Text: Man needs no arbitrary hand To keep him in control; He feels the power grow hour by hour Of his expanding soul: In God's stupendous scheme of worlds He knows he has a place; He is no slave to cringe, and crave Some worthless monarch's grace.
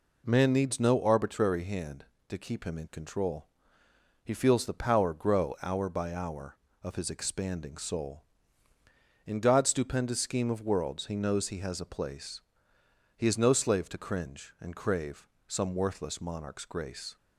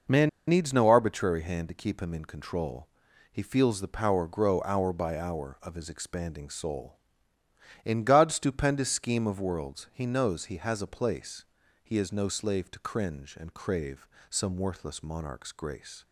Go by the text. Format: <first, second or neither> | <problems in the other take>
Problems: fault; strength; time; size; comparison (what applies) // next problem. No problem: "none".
first | pauses between "Man" and "needs"; slight; at 0.2 s; 0.19 s long // pauses between "crave" and "Some"; slight; at 14.0 s; 0.24 s long; slight in the first